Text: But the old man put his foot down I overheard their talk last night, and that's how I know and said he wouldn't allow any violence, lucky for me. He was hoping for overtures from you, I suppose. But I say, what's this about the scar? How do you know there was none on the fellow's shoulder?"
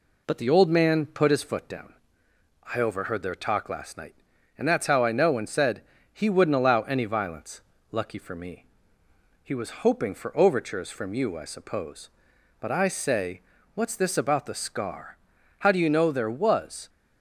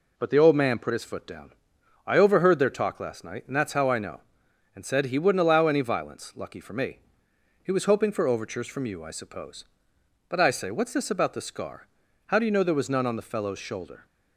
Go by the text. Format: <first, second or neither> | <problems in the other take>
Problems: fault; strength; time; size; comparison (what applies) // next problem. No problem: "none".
second | pauses between "down" and "I"; noticeable; at 1.9 s; 0.80 s long; noticeable in the second // pauses between "said" and "he"; slight; at 5.8 s; 0.30 s long // stops before "none on the fellow's shoulder"; at 16.8 s